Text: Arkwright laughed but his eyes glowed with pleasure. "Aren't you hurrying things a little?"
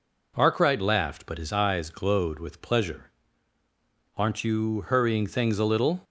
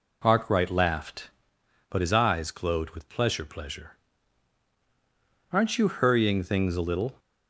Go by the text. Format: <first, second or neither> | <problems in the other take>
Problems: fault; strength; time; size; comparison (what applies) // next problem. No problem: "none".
first | says "pleasure" twice; at 3.4 s